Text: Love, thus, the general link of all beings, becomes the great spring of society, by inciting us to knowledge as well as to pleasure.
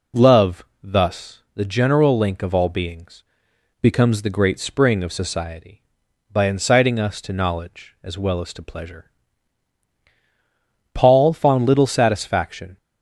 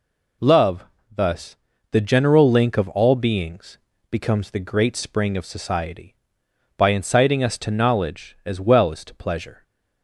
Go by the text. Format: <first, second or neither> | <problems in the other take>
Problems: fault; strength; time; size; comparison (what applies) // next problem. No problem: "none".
second | goes on to say "Paul found little satisfaction"; strong; from 10.9 s on; 1.8 s long